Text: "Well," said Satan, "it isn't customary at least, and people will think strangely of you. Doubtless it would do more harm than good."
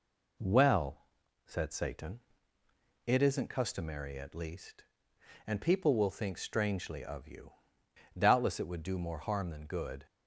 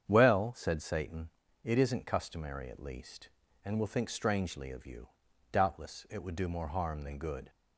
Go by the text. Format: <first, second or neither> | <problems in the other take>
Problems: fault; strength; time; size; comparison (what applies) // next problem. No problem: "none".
first | starts louder than the rest; strong; until 1.0 s; 8 dB // skips "people"; at 3.7 s